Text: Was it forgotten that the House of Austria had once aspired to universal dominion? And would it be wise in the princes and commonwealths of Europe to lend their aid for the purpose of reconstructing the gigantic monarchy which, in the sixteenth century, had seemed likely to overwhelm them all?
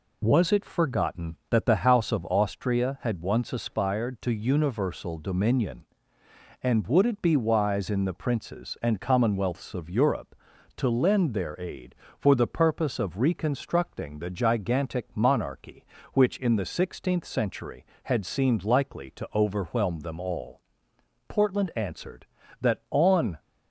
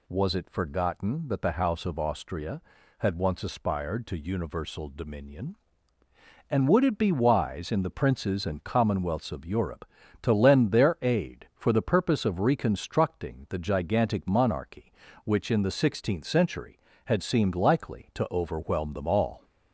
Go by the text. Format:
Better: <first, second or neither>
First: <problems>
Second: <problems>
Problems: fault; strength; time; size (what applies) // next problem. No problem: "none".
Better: second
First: goes on to say "Portland answered that on"; strong; from 21.2 s on; 2.1 s long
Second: none